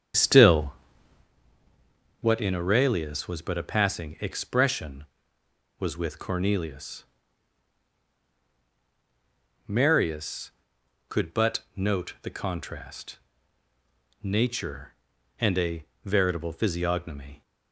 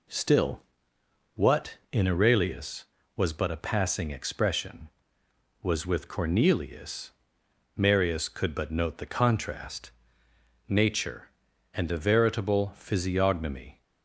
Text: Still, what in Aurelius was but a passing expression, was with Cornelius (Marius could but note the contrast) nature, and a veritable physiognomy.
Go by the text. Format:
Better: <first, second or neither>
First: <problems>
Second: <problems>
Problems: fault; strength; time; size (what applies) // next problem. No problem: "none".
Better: second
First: starts louder than the rest; strong; until 1.3 s; 8.5 dB // pauses between "but" and "note"; slight; at 11.5 s; 0.16 s long // pauses between "a" and "veritable"; slight; at 15.8 s; 0.22 s long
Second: none